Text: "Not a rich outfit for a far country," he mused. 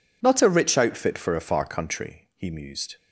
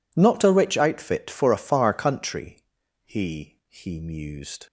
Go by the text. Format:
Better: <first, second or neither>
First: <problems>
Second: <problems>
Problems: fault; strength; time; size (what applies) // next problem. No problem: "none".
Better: first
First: none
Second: says "he" twice; at 3.7 s